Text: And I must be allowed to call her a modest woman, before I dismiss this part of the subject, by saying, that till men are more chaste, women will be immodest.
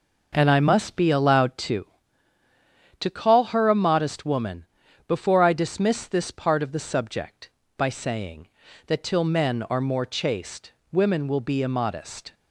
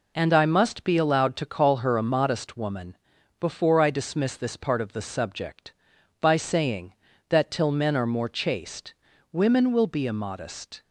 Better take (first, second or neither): second